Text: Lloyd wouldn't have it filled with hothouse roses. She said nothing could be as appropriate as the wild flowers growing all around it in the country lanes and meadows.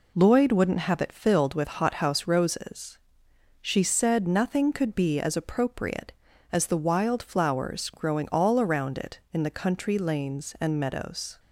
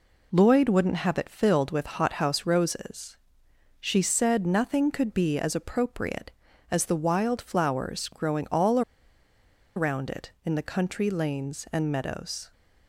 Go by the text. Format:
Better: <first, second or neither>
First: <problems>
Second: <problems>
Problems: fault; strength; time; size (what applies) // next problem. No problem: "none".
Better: first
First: none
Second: pauses between "all" and "around"; noticeable; at 8.8 s; 0.95 s long